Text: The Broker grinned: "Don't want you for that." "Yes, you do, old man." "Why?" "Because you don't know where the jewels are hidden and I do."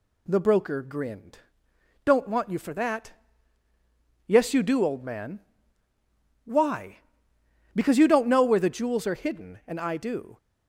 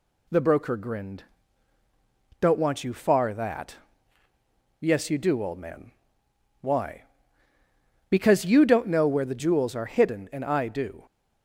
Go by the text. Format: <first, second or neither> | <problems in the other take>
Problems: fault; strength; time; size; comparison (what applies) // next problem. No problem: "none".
first | says "far" for "for"; at 2.9 s